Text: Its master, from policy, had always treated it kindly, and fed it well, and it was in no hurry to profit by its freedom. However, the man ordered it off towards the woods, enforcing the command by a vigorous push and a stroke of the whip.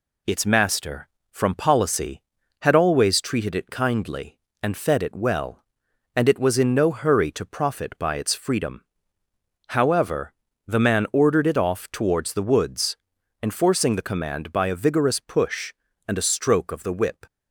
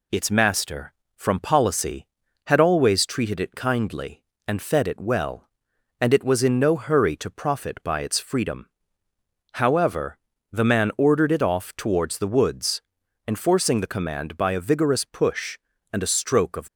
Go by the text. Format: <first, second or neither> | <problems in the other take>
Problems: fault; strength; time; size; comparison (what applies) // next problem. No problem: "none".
first | stops before "the whip"; at 16.6 s